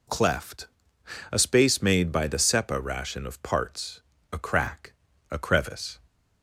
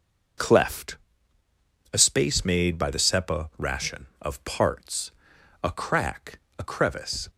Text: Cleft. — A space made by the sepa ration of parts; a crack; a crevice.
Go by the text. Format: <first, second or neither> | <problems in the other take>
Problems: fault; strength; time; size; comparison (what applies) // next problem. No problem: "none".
neither | none